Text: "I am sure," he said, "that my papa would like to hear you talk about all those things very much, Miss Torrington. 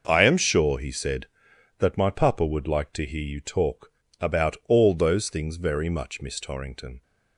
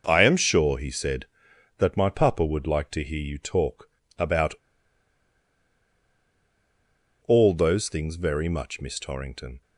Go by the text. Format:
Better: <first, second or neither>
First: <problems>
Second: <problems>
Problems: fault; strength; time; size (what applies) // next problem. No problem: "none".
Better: first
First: pauses between "talk" and "about"; slight; at 3.9 s; 0.30 s long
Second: pauses between "talk" and "about"; slight; at 3.8 s; 0.30 s long // pauses between "about" and "all"; strong; at 4.5 s; 2.7 s long